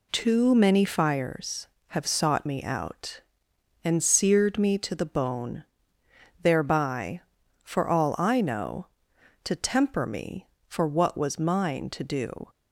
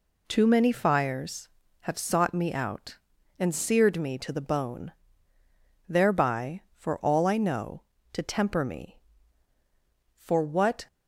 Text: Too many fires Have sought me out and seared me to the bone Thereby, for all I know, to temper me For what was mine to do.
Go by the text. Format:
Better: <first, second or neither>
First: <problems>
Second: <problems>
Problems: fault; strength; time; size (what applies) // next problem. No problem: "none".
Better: first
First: pauses between "bone" and "Thereby"; noticeable; at 5.6 s; 0.76 s long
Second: pauses between "bone" and "Thereby"; noticeable; at 4.9 s; 0.96 s long // stops before "was mine to do"; at 10.8 s